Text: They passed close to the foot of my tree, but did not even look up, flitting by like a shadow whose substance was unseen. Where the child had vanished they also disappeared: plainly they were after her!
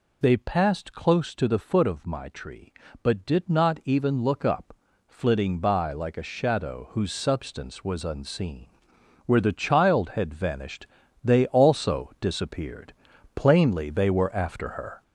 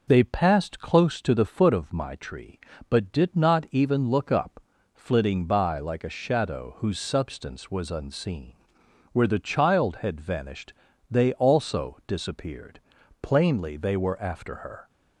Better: second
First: gets louder; noticeable; throughout; 4.5 dB // pauses between "vanished" and "they"; at 10.8 s; 0.38 s long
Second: pauses between "vanished" and "they"; at 10.7 s; 0.38 s long

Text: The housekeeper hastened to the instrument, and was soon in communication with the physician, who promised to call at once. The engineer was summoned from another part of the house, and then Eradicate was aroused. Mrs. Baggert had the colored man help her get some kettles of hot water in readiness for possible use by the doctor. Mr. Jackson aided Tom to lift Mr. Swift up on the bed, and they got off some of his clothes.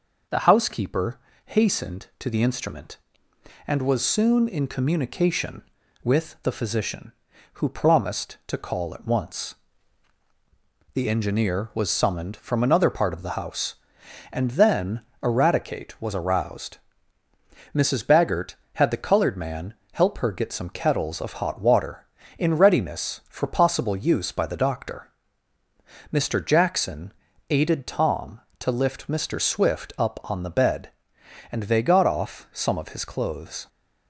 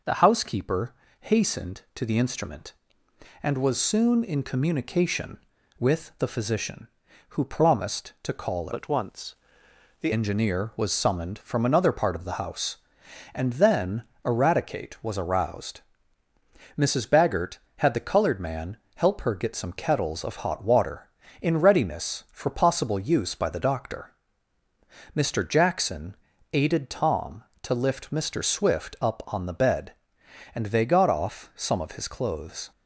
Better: first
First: pauses between "housekeeper" and "hastened"; slight; at 1.1 s; 0.26 s long // pauses between "then" and "Eradicate"; slight; at 15.0 s; 0.22 s long // pauses between "man" and "help"; slight; at 19.7 s; 0.18 s long // pauses between "Jackson" and "aided"; at 27.1 s; 0.38 s long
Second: pauses between "housekeeper" and "hastened"; slight; at 0.9 s; 0.26 s long // changes voice from "at" to "The"; from 8.7 to 10.1 s; 1.4 s long // pauses between "then" and "Eradicate"; slight; at 14.0 s; 0.22 s long // pauses between "man" and "help"; slight; at 18.7 s; 0.18 s long // pauses between "Jackson" and "aided"; at 26.1 s; 0.38 s long

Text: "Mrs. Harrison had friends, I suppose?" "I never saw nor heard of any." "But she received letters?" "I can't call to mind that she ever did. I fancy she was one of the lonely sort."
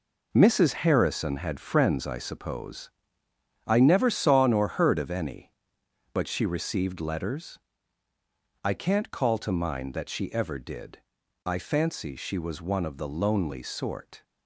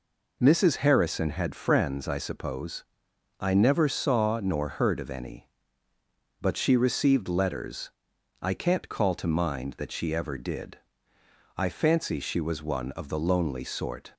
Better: second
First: gets quieter; strong; throughout; 8.5 dB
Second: none

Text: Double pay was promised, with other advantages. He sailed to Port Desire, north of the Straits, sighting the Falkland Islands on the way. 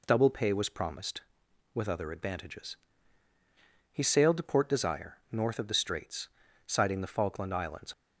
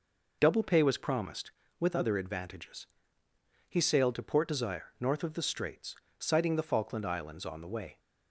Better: second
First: stops before "on the way"; at 7.9 s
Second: none

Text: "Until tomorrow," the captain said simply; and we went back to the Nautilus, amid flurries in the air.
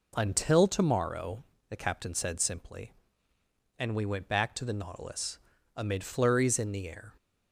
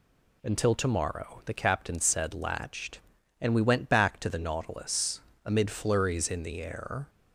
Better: first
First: none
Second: says "latched" for "simply"; at 2.3 s

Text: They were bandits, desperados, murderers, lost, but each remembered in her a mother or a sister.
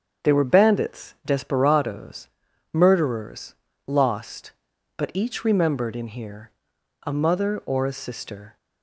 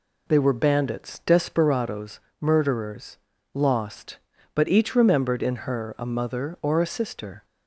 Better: second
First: starts louder than the rest; strong; until 1.3 s; 7.5 dB // says "here" for "her"; at 6.0 s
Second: none

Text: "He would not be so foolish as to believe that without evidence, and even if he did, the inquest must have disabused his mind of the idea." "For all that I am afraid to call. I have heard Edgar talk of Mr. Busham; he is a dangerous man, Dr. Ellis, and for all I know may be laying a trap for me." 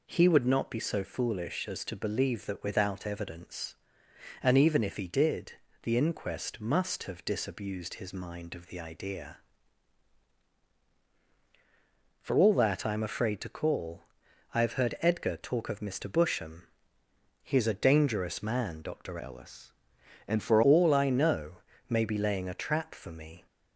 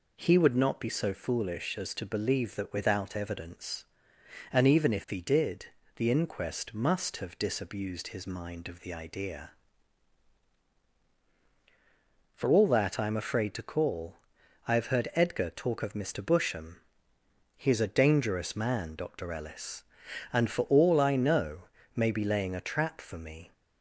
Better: second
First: changes voice from "Ellis" to "for"; from 19.2 to 20.6 s; 1.4 s long // pauses between "know" and "may"; slight; at 21.5 s; 0.32 s long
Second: pauses between "know" and "may"; slight; at 21.6 s; 0.32 s long

